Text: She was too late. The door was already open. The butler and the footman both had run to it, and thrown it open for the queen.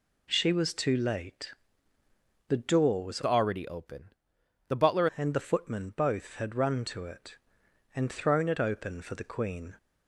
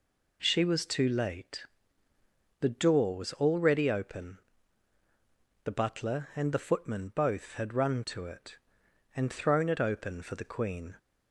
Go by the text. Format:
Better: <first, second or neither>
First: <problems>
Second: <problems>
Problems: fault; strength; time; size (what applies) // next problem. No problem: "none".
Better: second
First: changes voice from "already" to "butler"; from 3.2 to 5.0 s; 1.8 s long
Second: none